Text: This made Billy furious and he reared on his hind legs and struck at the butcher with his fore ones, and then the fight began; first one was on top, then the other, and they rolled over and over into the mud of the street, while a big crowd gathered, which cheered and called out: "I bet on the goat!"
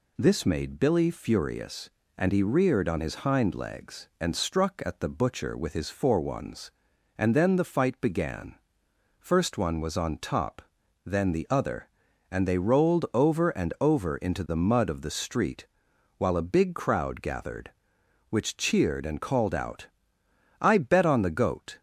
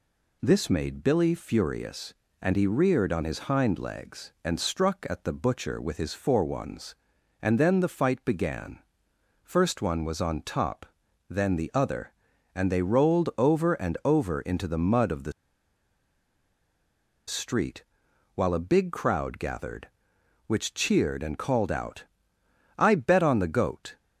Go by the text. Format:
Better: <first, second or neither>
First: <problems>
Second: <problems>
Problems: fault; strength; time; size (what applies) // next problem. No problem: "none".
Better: first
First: none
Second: pauses between "the" and "street"; strong; at 15.3 s; 1.9 s long